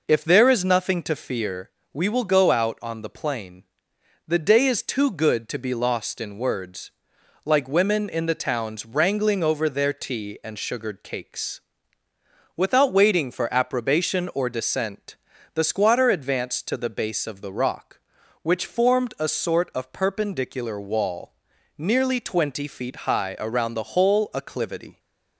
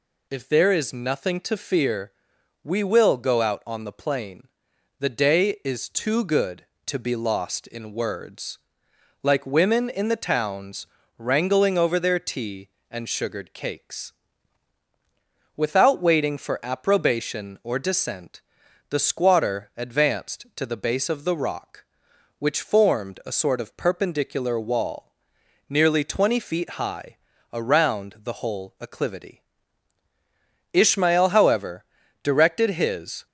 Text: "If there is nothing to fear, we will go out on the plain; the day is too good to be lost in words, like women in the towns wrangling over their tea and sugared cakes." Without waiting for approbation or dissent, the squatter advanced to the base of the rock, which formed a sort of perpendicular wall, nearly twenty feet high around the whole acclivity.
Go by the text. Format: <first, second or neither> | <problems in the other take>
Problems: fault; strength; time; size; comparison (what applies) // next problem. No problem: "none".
first | pauses between "towns" and "wrangling"; slight; at 10.8 s; 0.32 s long // pauses between "high" and "around"; at 27.1 s; 0.38 s long // goes on to say "Ishmael however directed his"; strong; from 30.7 s on; 2.5 s long